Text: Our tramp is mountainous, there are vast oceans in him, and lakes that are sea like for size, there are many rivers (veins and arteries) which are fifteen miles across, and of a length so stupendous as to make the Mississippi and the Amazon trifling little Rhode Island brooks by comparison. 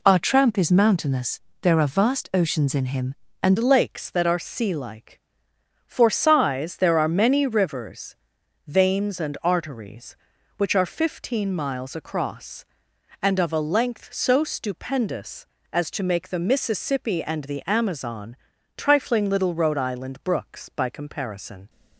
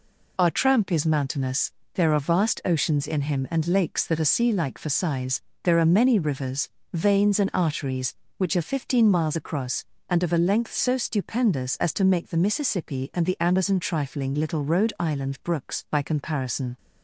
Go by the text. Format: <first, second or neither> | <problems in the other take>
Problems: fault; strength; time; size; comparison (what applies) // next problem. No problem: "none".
second | changes voice at "lakes"; from 3.5 s on; 18.1 s long // pauses between "Amazon" and "trifling"; at 18.3 s; 0.40 s long